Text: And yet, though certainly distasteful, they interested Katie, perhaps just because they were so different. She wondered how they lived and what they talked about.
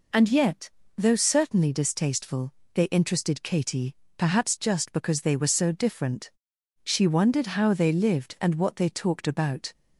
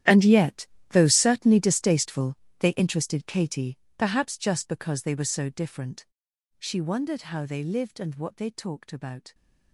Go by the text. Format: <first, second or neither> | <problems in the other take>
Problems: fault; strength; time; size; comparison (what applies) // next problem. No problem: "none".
first | gets quieter; strong; throughout; 17 dB